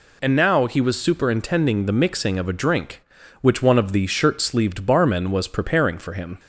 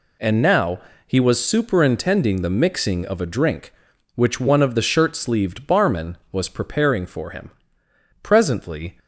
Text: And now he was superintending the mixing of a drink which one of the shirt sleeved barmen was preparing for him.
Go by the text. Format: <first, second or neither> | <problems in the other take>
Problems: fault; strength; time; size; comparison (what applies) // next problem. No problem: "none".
first | pauses between "now" and "he"; slight; at 0.8 s; 0.26 s long // goes on to say "Presently"; noticeable; from 8.2 s on; 0.76 s long